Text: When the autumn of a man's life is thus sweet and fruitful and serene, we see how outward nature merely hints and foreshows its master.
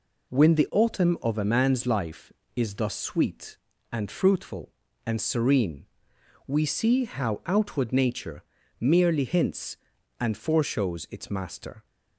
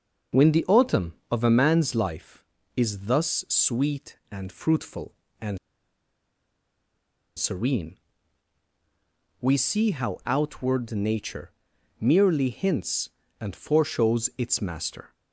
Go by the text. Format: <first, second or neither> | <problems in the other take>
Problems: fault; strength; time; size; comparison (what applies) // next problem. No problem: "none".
first | starts louder than the rest; until 1.5 s; 6.5 dB // pauses between "and" and "serene"; strong; at 5.5 s; 1.8 s long // pauses between "nature" and "merely"; noticeable; at 11.5 s; 0.50 s long; also in the first